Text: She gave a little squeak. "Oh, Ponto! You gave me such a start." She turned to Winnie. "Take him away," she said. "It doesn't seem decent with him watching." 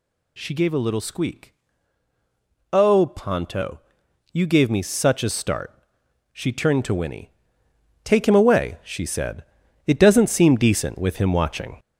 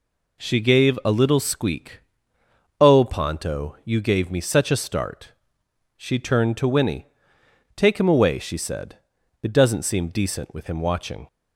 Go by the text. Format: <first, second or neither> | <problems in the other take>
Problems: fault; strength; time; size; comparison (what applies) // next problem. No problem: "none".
second | gets louder; noticeable; throughout; 5 dB